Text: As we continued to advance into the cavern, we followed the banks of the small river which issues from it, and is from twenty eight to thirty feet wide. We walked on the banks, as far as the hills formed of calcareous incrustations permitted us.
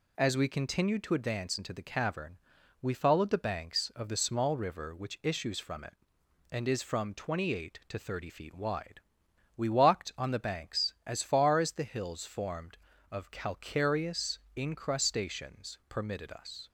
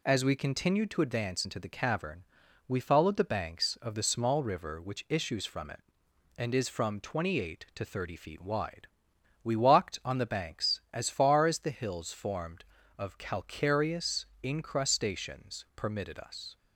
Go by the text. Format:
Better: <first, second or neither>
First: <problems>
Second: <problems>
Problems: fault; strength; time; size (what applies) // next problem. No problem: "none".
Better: neither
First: pauses between "calcareous" and "incrustations"; slight; at 14.3 s; 0.18 s long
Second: pauses between "calcareous" and "incrustations"; slight; at 14.2 s; 0.18 s long